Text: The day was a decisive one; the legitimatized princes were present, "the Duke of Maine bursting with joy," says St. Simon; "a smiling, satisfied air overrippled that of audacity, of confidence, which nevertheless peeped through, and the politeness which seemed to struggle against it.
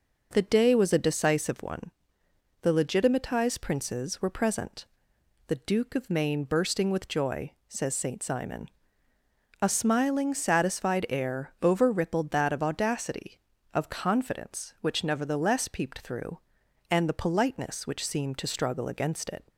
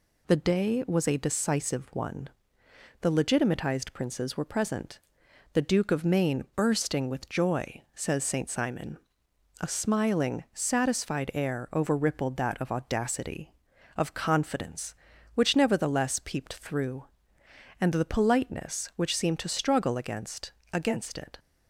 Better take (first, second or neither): first